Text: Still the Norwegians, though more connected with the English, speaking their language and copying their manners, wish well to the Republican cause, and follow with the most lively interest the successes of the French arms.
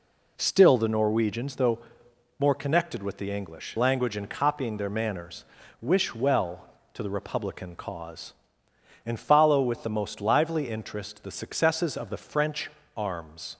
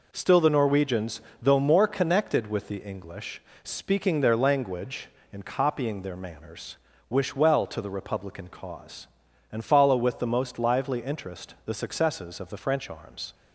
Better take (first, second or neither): second